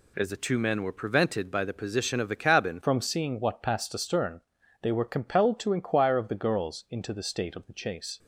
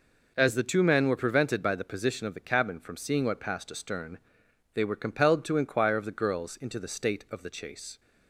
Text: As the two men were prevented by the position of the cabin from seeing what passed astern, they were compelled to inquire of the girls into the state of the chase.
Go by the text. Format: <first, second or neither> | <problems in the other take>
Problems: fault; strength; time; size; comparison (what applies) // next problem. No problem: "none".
second | changes voice at "from"; from 2.8 s on; 5.3 s long